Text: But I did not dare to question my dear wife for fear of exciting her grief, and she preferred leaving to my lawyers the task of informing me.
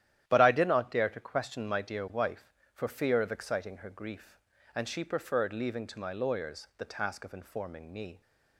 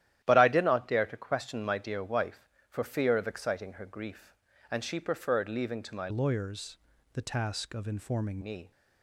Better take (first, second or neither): first